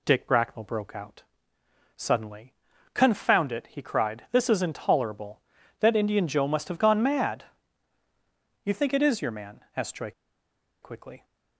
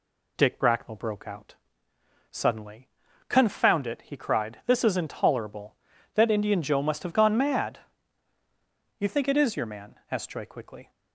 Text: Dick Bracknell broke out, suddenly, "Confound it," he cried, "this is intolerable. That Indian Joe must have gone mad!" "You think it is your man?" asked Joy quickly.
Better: second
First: pauses between "Joy" and "quickly"; noticeable; at 10.1 s; 0.71 s long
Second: none

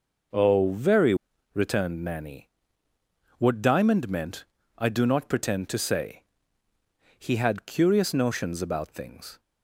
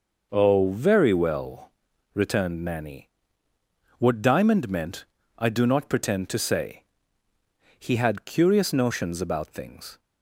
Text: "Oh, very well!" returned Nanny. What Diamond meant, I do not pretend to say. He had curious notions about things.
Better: second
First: skips "well"; at 1.3 s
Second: none

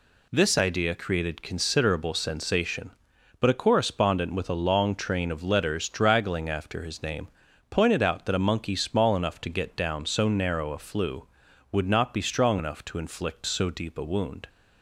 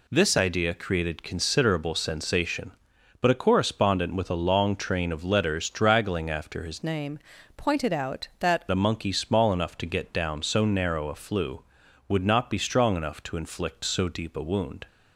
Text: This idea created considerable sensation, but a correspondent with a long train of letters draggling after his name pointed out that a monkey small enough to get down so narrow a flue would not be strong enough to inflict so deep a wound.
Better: first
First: pauses between "name" and "pointed"; at 7.2 s; 0.42 s long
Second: changes voice from "name" to "that"; from 6.8 to 8.6 s; 1.8 s long // pauses between "name" and "pointed"; at 7.1 s; 0.38 s long

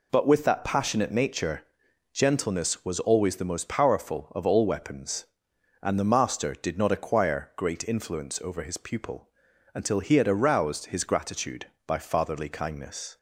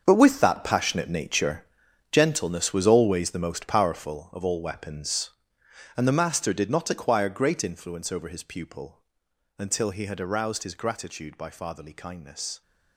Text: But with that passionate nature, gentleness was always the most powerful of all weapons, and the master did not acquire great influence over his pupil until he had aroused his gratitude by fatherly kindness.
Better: first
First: pauses between "pupil" and "until"; at 9.2 s; 0.44 s long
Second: gets quieter; strong; throughout; 13.5 dB // pauses between "pupil" and "until"; noticeable; at 9.0 s; 0.54 s long

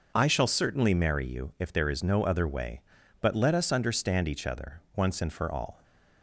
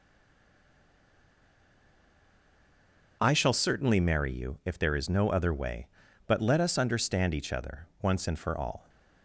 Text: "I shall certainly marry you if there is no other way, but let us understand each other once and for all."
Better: first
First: starts louder than the rest; noticeable; until 1.1 s; 6 dB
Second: stays silent before the first word; strong; until 3.2 s; 3.2 s long // starts louder than the rest; noticeable; until 4.2 s; 6 dB

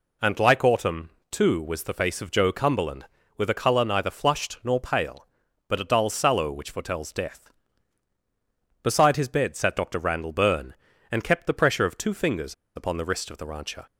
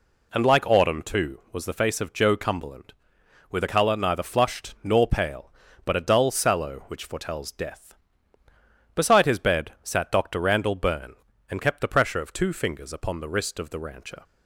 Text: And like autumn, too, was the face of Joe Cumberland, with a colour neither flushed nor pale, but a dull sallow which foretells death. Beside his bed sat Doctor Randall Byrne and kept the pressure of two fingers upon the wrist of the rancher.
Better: second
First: pauses between "fingers" and "upon"; slight; at 12.5 s; 0.21 s long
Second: none

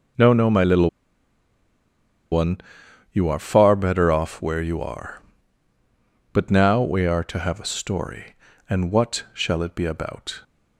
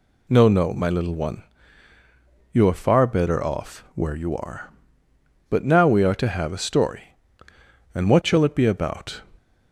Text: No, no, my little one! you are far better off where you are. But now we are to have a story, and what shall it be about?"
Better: second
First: pauses between "little" and "one"; strong; at 0.8 s; 1.4 s long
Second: none

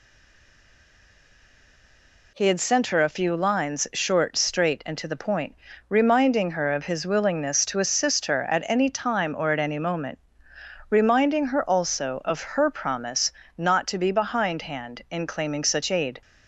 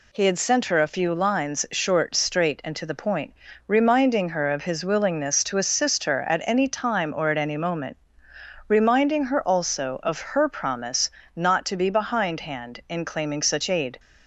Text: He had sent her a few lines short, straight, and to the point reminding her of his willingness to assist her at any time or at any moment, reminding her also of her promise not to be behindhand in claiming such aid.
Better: second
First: stays silent before the first word; until 2.3 s; 2.3 s long // pauses between "point" and "reminding"; slight; at 5.5 s; 0.32 s long // pauses between "promise" and "not"; slight; at 13.3 s; 0.24 s long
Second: pauses between "point" and "reminding"; slight; at 3.3 s; 0.32 s long // pauses between "promise" and "not"; slight; at 11.0 s; 0.24 s long

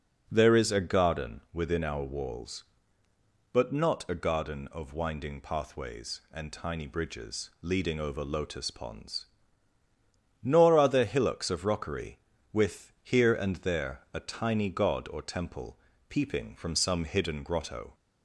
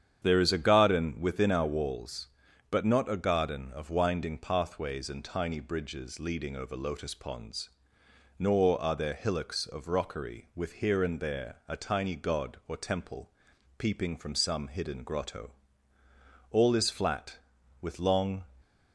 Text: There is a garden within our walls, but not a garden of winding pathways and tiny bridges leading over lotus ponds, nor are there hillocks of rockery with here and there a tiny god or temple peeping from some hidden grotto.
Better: first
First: pauses between "temple" and "peeping"; slight; at 15.7 s; 0.32 s long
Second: starts louder than the rest; strong; until 1.2 s; 8.5 dB // pauses between "temple" and "peeping"; noticeable; at 13.3 s; 0.46 s long // goes on to say "All is flat with long"; strong; from 16.5 s on; 1.9 s long

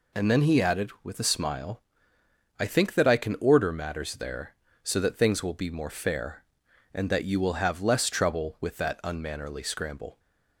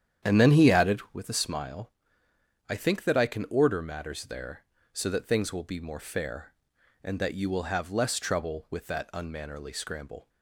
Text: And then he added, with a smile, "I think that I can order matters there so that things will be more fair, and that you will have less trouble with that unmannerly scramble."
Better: first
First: none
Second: starts louder than the rest; strong; until 1.3 s; 9.5 dB

